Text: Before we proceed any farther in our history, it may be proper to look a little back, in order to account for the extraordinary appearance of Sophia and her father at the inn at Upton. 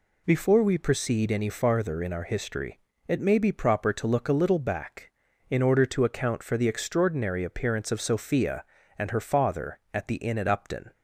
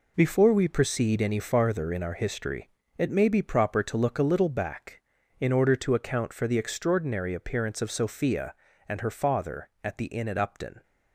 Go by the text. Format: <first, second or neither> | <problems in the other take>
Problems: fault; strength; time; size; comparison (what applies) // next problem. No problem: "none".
first | gets quieter; strong; throughout; 8.5 dB